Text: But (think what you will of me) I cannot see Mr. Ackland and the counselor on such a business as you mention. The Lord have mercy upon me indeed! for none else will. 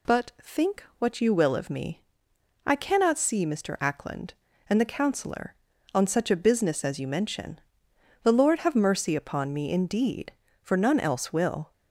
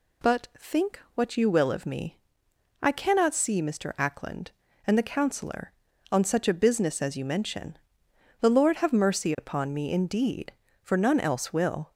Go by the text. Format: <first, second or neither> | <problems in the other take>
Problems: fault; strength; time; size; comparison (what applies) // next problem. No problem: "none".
neither | none